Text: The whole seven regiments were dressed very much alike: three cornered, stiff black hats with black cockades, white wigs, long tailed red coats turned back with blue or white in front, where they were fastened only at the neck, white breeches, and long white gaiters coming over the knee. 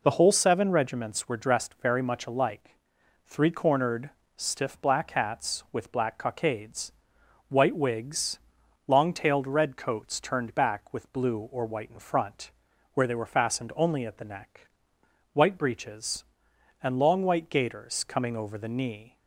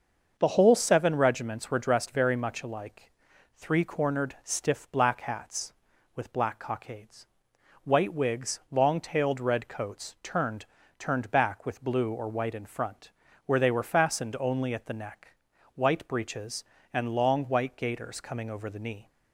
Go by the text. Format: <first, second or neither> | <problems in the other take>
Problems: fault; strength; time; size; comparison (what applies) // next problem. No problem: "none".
first | starts louder than the rest; until 1.3 s; 6.5 dB // says "turned" twice; at 10.9 s